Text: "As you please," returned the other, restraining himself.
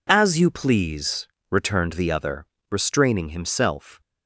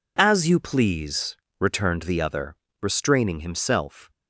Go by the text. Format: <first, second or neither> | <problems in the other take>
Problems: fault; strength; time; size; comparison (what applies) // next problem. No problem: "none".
neither | none